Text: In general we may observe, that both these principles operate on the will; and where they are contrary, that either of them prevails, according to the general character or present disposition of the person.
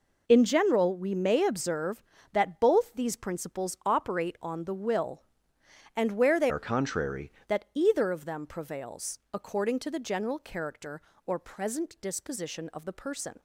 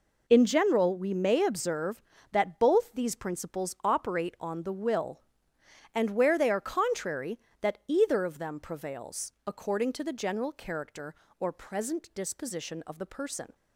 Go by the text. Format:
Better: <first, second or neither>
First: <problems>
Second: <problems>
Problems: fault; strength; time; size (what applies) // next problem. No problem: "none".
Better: second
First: changes voice from "are" to "contrary"; from 6.4 to 7.3 s; 0.9 s long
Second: none